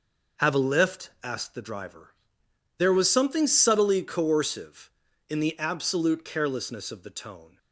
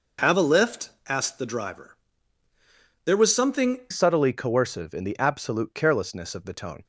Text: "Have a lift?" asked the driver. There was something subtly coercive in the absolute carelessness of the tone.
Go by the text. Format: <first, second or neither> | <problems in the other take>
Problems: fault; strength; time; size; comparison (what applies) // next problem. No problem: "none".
first | changes voice at "subtly"; from 3.9 s on; 2.9 s long